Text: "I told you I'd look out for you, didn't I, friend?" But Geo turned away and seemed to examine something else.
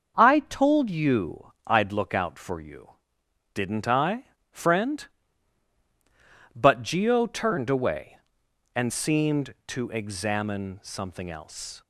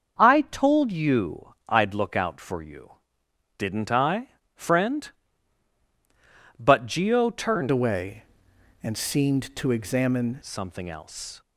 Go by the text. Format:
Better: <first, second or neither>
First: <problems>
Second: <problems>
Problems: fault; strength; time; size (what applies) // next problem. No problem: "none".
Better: first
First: starts louder than the rest; until 1.2 s; 6.5 dB // pauses between "you" and "I'd"; slight; at 1.5 s; 0.16 s long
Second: starts louder than the rest; until 1.2 s; 7 dB // pauses between "you" and "I'd"; slight; at 1.5 s; 0.16 s long // changes voice from "away" to "examine"; from 7.7 to 10.4 s; 2.7 s long